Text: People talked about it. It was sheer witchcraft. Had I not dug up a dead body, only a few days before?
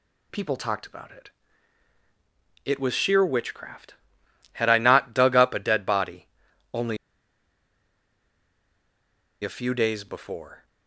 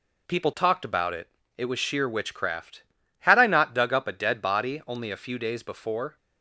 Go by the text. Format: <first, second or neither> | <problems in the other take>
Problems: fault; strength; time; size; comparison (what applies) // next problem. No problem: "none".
second | pauses between "only" and "a"; strong; at 6.9 s; 2.4 s long